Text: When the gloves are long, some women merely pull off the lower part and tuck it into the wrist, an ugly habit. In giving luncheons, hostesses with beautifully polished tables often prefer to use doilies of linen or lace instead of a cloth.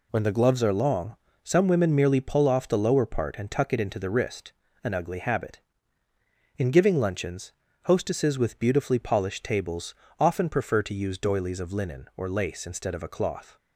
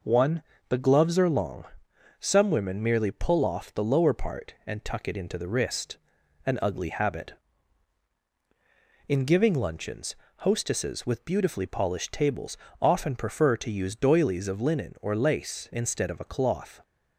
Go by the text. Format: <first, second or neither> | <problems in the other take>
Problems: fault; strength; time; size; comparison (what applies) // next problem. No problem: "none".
first | says "One" for "When"; at 0.0 s // pauses between "tables" and "often"; slight; at 12.5 s; 0.24 s long; slight in the first